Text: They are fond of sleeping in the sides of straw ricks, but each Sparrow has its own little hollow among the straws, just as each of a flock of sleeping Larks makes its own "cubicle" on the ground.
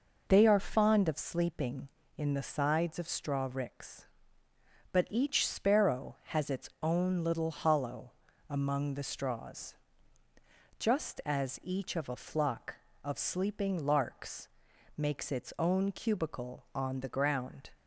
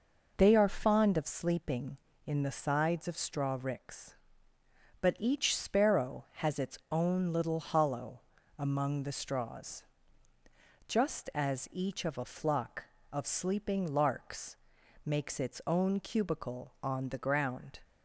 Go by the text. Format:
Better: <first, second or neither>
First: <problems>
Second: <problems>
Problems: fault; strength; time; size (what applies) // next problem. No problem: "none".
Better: neither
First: pauses between "hollow" and "among"; at 8.1 s; 0.38 s long // pauses between "Larks" and "makes"; noticeable; at 14.4 s; 0.48 s long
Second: pauses between "hollow" and "among"; at 8.1 s; 0.38 s long // pauses between "Larks" and "makes"; noticeable; at 14.5 s; 0.48 s long